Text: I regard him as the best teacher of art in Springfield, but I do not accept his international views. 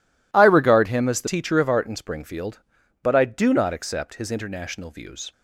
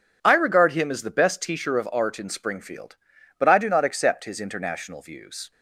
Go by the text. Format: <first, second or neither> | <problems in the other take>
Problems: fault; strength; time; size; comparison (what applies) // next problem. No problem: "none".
second | skips "best"; at 1.2 s